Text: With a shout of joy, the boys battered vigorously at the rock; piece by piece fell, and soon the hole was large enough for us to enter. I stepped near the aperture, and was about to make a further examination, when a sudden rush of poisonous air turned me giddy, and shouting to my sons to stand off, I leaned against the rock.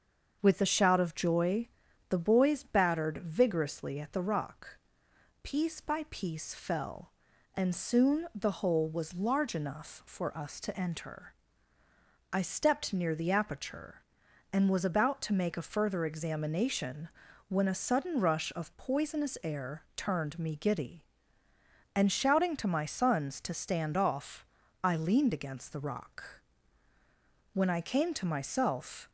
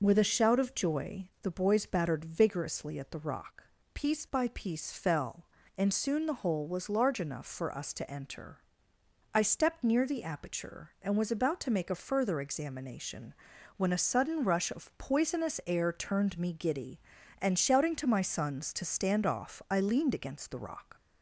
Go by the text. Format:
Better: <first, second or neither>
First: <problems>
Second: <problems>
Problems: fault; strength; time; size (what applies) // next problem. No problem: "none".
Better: second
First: starts louder than the rest; until 1.4 s; 6.5 dB // goes on to say "When I came to myself"; from 27.5 s on; 1.5 s long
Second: none